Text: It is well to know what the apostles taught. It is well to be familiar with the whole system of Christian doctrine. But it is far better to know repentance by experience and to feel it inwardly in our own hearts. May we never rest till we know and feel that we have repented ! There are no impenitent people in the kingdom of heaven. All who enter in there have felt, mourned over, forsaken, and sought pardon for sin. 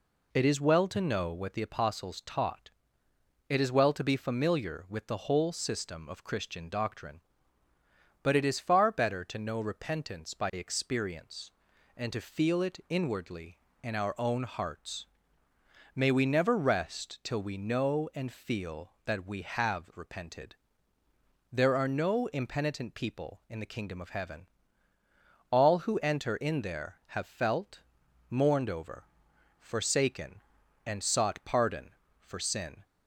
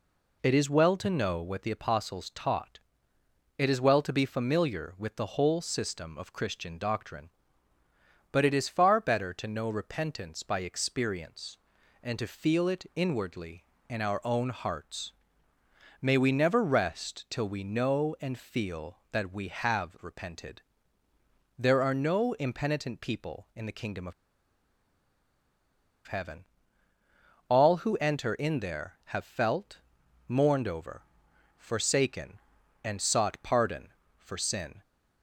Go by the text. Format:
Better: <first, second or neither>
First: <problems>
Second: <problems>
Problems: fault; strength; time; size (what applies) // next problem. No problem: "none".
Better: first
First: none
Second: pauses between "of" and "heaven"; strong; at 24.1 s; 1.9 s long